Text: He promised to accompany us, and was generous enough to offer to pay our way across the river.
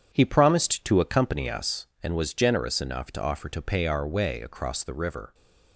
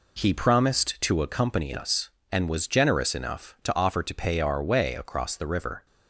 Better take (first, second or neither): second